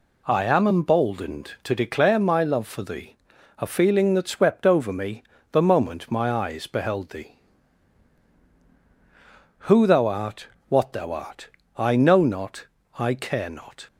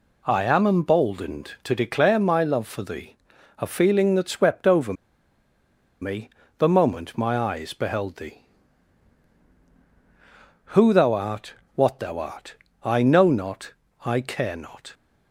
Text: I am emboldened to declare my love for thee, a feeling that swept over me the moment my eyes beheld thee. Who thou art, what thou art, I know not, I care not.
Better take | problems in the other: first | pauses between "over" and "me"; at 4.9 s; 1.0 s long // pauses between "me" and "the"; slight; at 6.2 s; 0.28 s long; slight in the first

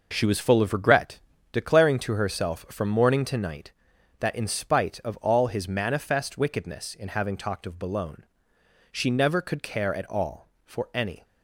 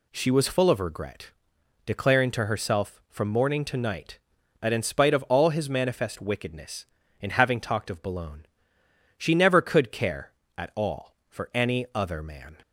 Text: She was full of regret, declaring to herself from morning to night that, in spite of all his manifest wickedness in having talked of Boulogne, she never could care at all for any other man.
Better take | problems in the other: second | stops before "other man"; at 11.2 s

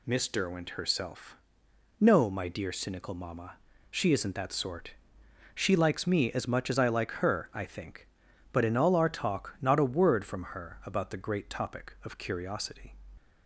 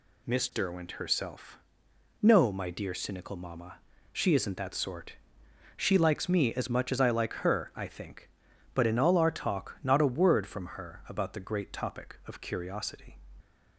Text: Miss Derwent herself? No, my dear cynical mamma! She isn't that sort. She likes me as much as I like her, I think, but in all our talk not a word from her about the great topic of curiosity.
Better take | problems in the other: neither | none

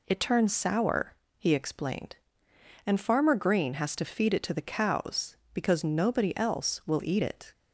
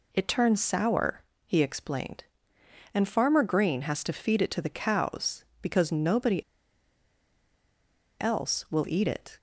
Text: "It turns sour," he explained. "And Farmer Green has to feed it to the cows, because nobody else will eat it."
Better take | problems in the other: first | pauses between "nobody" and "else"; strong; at 6.4 s; 1.7 s long

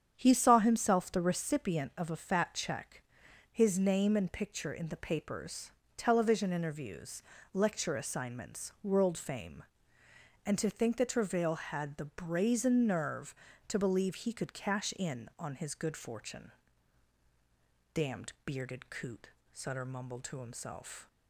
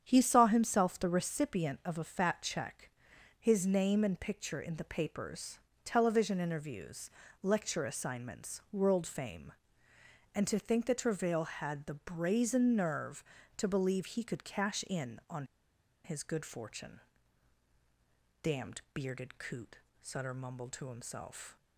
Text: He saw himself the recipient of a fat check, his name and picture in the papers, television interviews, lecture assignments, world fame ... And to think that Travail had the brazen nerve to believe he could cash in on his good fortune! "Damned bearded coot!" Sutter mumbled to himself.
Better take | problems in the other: first | starts louder than the rest; strong; until 1.0 s; 8.5 dB; strong in the first // pauses between "on" and "his"; noticeable; at 15.4 s; 0.60 s long

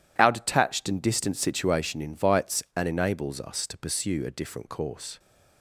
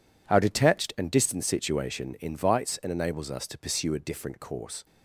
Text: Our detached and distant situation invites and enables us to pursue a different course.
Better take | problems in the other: neither | none

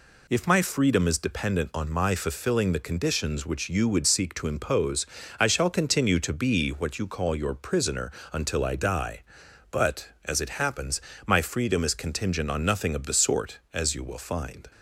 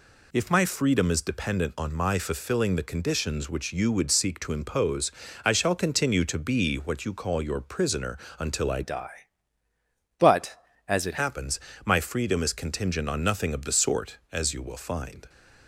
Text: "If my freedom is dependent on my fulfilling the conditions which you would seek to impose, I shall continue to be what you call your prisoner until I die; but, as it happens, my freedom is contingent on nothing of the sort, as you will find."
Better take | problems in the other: first | pauses between "prisoner" and "until"; slight; at 8.1 s; 0.22 s long; slight in the first // changes voice from "die" to "it"; from 8.8 to 11.1 s; 2.3 s long

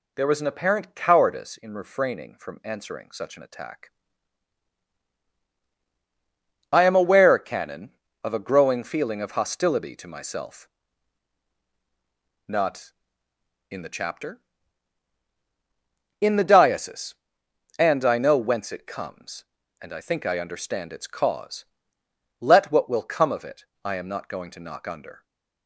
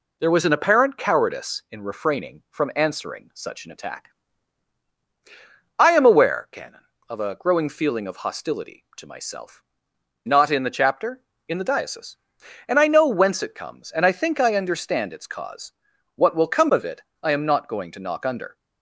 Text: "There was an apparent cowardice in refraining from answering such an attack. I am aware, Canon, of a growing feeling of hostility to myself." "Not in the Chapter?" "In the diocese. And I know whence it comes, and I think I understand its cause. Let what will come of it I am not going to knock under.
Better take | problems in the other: first | skips "Let"; at 15.9 s // pauses between "it" and "I"; slight; at 17.0 s; 0.20 s long; slight in the first

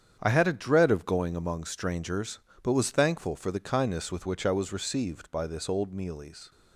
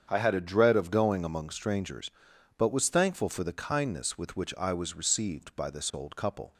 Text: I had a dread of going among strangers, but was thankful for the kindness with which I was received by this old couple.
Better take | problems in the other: second | starts louder than the rest; strong; until 1.2 s; 8 dB; strong in the second // says "mealies" for "couple"; at 5.9 s

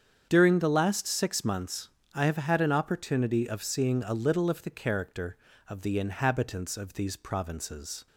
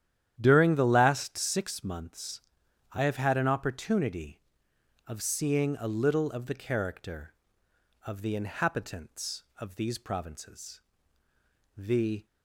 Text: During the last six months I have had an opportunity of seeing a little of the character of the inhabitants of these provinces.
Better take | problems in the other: first | starts louder than the rest; strong; until 1.3 s; 10.5 dB; strong in the first // pauses between "months" and "I"; noticeable; at 2.4 s; 0.50 s long; slight in the first // goes on to say "The"; slight; from 11.7 s on; 0.48 s long

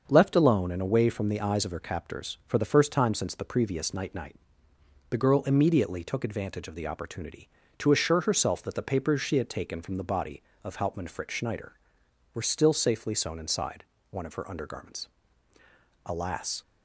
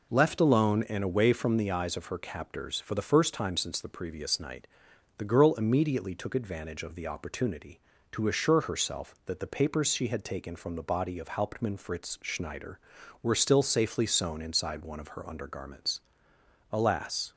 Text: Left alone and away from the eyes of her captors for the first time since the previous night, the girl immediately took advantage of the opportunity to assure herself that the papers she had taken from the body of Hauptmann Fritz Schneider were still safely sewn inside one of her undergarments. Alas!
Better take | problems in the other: second | starts louder than the rest; until 1.0 s; 6.5 dB // says "night" twice; at 4.1 s // pauses between "inside" and "one"; slight; at 13.8 s; 0.28 s long

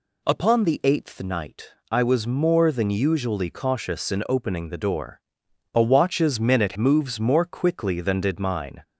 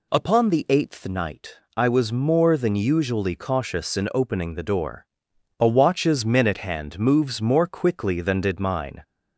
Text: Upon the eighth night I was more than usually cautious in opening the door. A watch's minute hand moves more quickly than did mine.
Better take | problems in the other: second | pauses between "night" and "I"; slight; at 1.7 s; 0.18 s long; slight in the second // skips "hand"; at 6.7 s

